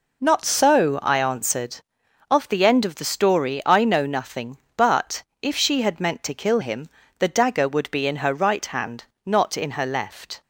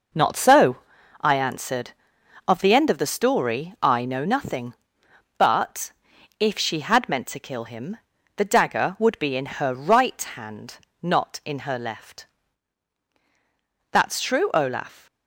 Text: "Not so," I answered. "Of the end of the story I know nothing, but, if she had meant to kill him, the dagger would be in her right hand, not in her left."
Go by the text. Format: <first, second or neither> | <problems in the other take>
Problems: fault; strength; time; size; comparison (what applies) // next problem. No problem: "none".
first | goes on to say "That's true Olaf"; noticeable; from 13.9 s on; 1.1 s long